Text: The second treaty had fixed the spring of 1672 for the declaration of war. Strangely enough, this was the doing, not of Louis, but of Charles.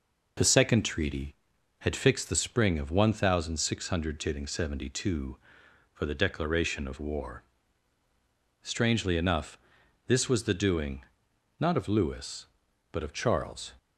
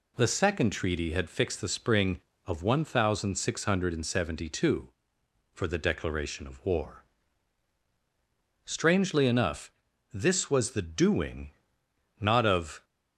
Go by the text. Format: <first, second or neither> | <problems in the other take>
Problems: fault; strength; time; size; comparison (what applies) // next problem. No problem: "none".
first | stops before "Louis but of Charles"; at 12.8 s